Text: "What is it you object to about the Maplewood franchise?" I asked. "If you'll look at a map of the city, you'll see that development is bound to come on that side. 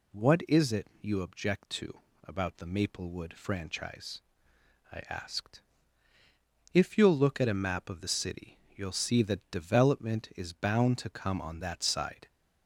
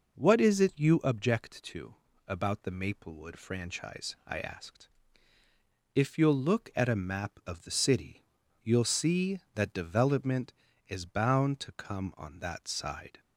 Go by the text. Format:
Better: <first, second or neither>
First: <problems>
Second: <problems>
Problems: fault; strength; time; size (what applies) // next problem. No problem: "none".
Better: neither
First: pauses between "to" and "about"; slight; at 1.9 s; 0.24 s long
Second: pauses between "to" and "about"; slight; at 1.9 s; 0.32 s long